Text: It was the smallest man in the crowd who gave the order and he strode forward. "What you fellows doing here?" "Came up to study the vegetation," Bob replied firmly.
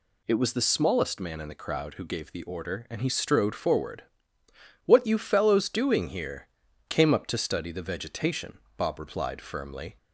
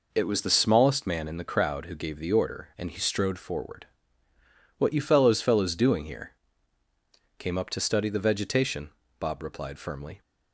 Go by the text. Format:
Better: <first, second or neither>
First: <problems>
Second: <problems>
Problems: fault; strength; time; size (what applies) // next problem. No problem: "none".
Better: first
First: none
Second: says "fellows" twice; at 5.4 s